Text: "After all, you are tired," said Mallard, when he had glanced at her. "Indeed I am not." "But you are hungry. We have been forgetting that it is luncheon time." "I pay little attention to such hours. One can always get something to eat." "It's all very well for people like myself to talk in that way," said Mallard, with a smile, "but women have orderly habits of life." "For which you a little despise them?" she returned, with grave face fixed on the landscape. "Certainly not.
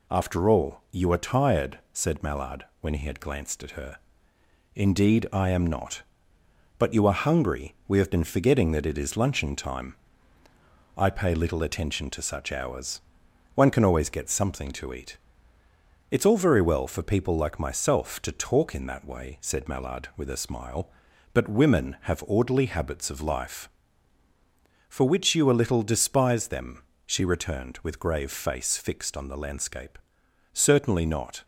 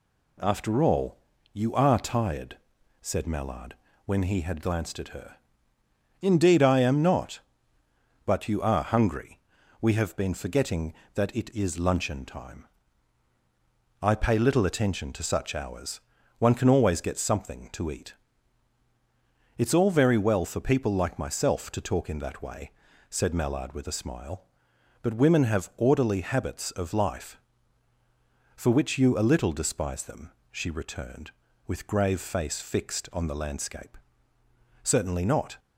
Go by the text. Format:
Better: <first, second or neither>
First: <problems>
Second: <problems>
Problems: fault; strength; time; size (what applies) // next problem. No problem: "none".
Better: neither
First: none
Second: none